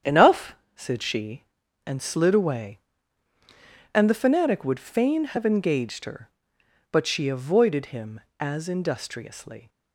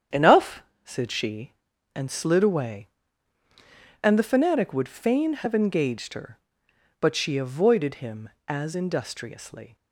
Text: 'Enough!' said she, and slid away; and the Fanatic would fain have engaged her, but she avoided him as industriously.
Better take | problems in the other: neither | starts louder than the rest; strong; the same in both

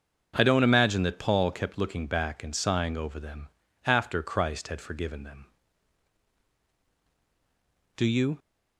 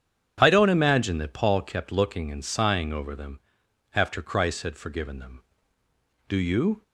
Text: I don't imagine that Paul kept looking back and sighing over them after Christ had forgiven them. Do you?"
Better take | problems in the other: first | starts louder than the rest; strong; until 1.4 s; 8 dB; also in the first // skips "back"; at 2.3 s // pauses between "them" and "after"; noticeable; at 3.4 s; 0.52 s long; also in the first

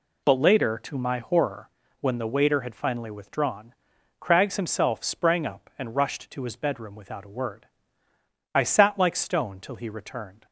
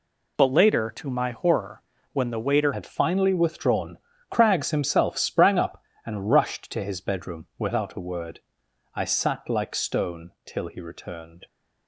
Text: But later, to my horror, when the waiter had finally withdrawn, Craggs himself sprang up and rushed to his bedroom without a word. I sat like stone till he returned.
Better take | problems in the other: first | changes voice at "had"; from 2.7 s on; 8.7 s long

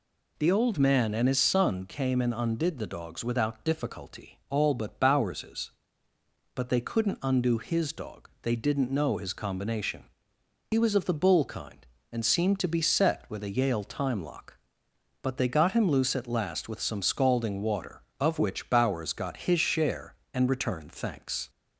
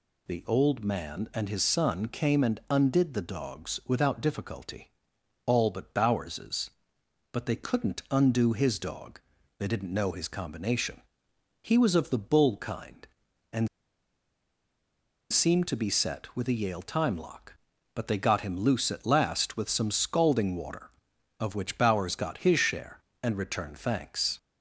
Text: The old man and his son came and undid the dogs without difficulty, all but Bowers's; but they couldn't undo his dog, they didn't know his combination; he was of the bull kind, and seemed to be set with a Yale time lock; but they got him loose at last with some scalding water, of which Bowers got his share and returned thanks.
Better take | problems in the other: first | pauses between "and" and "seemed"; strong; at 13.6 s; 1.6 s long

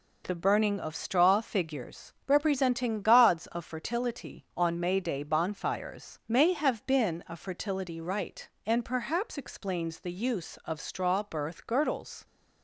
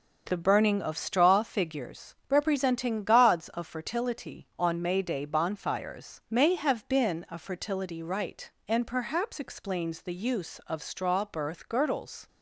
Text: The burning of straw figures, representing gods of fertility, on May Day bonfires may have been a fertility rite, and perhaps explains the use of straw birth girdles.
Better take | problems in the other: first | starts louder than the rest; until 1.5 s; 6 dB

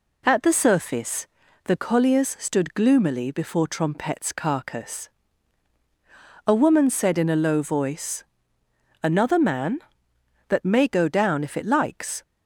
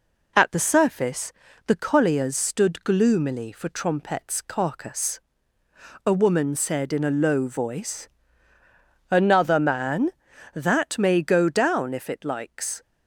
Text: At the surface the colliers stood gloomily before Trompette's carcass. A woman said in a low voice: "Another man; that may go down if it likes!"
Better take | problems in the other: first | pauses between "surface" and "the"; slight; at 1.3 s; 0.36 s long; also in the first // says "for" for "before"; at 3.5 s

